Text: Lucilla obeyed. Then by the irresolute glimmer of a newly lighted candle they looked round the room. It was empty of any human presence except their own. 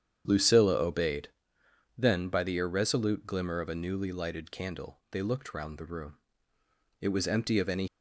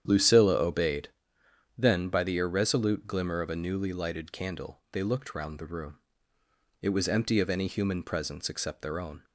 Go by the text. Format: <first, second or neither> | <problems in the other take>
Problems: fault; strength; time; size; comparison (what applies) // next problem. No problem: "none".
second | starts louder than the rest; strong; until 1.2 s; 8.5 dB; strong in the second // stops before "human presence except their own"; at 7.8 s